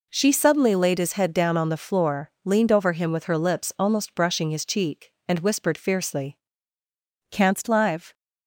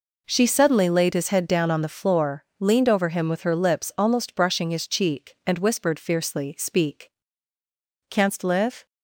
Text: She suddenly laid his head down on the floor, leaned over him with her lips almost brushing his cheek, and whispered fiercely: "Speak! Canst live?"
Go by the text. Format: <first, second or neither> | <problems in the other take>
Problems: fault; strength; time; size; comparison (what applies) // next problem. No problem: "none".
second | skips "Speak"; at 6.8 s